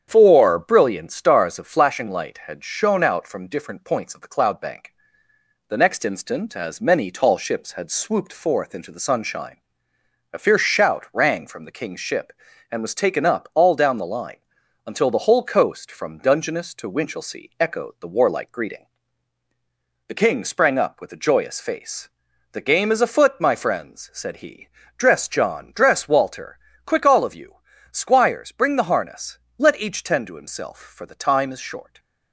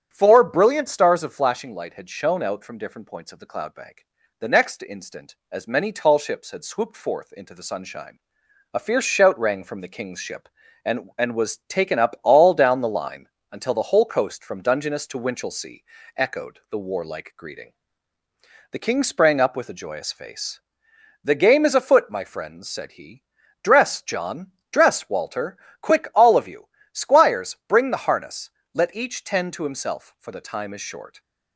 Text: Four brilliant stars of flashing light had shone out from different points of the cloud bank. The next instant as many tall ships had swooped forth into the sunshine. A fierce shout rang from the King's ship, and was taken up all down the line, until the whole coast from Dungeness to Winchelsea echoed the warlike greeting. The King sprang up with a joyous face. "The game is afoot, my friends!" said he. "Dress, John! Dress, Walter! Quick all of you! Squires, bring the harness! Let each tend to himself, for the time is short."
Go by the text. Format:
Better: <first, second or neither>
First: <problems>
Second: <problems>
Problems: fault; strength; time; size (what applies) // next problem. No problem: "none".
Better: first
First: starts louder than the rest; strong; until 1.0 s; 8.5 dB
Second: starts louder than the rest; strong; until 1.1 s; 9 dB // says "and" twice; at 11.1 s // pauses between "Winchelsea" and "echoed"; slight; at 15.8 s; 0.34 s long